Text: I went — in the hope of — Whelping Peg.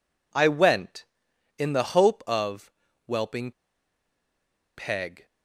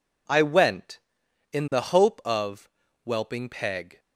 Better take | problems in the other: second | pauses between "Whelping" and "Peg"; strong; at 3.5 s; 1.2 s long

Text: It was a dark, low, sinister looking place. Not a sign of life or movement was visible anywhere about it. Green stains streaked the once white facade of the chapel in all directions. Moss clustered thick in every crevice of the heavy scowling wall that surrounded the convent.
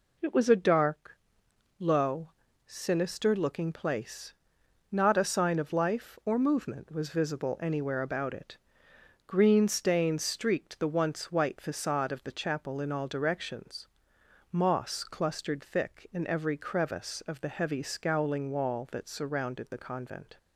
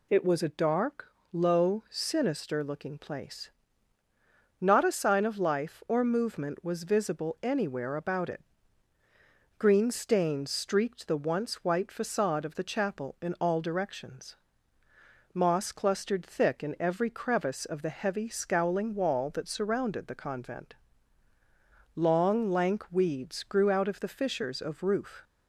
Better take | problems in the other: first | goes on to say "Long lank weeds grew out of the fissures of roof"; strong; from 21.9 s on; 3.3 s long

